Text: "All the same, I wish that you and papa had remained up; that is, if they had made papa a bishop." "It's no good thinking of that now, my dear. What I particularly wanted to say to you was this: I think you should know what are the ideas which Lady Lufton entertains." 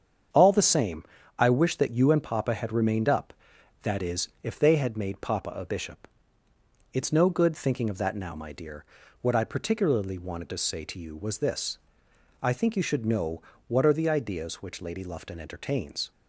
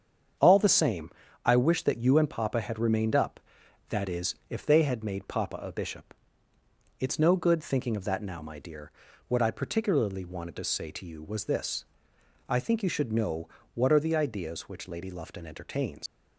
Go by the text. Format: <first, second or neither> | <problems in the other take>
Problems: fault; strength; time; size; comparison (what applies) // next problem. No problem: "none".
first | starts louder than the rest; strong; until 1.7 s; 7.5 dB; strong in the first // pauses between "know" and "what"; slight; at 13.4 s; 0.28 s long; slight in the first // leaves "entertains" unfinished; at 16.0 s; 115 ms